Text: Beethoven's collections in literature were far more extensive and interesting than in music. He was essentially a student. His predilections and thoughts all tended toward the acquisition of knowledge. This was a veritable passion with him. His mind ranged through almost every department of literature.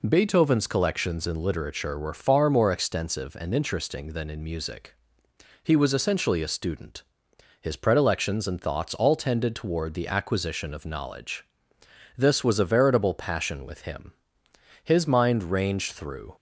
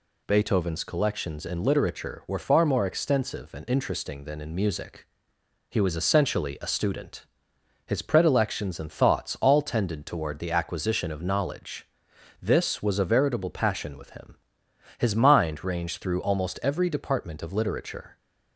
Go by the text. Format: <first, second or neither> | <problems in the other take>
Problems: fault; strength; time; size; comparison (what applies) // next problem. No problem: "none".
second | stops before "almost every department of literature"; at 16.3 s